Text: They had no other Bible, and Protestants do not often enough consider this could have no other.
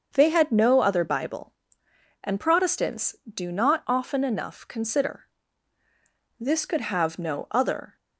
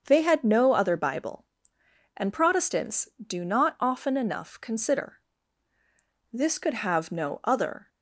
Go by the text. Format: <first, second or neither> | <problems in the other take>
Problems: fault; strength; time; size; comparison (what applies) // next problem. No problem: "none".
neither | starts louder than the rest; the same in both // pauses between "consider" and "this"; the same in both